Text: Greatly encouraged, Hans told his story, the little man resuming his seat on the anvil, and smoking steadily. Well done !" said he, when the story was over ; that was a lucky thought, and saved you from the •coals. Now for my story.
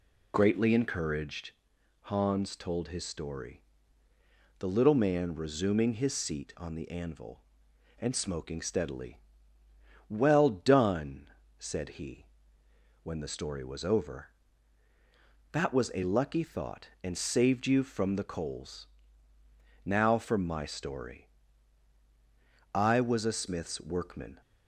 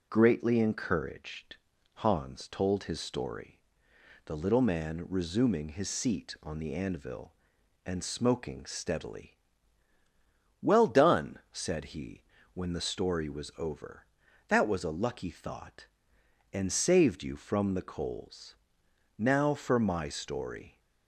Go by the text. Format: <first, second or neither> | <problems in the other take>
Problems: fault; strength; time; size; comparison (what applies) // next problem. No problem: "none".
second | goes on to say "I was a smith's workman"; strong; from 22.7 s on; 1.6 s long